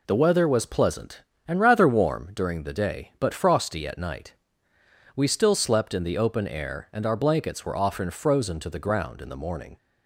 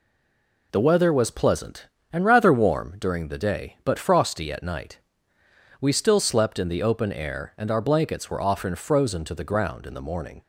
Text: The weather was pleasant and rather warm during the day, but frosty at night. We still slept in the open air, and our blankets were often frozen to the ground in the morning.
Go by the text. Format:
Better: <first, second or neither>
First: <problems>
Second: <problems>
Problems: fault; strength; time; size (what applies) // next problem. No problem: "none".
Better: first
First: none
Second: stays silent before the first word; slight; until 0.7 s; 0.7 s long